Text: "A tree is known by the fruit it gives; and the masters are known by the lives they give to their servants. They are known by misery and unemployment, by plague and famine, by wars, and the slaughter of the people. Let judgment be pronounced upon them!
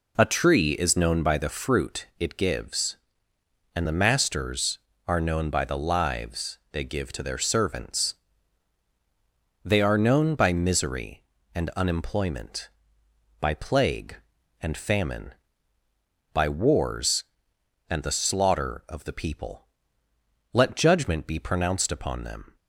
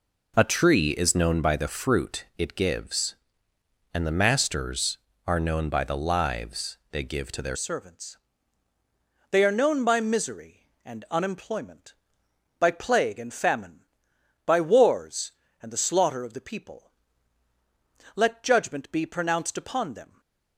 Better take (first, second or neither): first